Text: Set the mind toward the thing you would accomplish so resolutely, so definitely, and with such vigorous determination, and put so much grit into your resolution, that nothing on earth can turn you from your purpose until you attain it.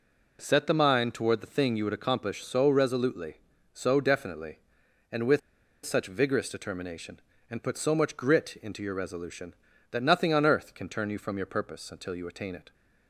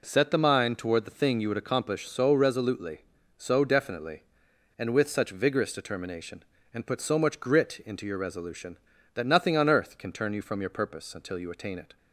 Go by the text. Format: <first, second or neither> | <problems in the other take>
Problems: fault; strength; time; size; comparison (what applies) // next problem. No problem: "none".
second | pauses between "with" and "such"; at 5.4 s; 0.45 s long